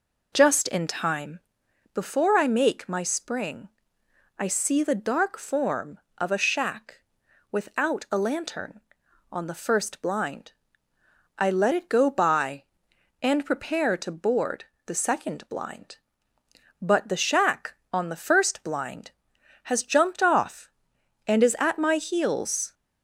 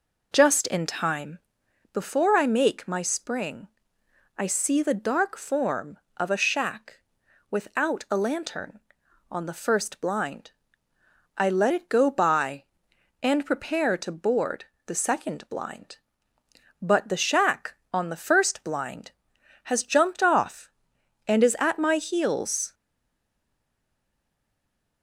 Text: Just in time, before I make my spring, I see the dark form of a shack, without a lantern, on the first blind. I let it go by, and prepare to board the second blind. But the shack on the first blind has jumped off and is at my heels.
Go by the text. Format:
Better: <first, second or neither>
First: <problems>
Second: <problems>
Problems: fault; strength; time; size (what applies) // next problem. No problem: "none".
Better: first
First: pauses between "board" and "the"; slight; at 14.6 s; 0.20 s long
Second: pauses between "board" and "the"; slight; at 14.6 s; 0.20 s long // stays silent after the last word; from 22.7 s on; 2.3 s long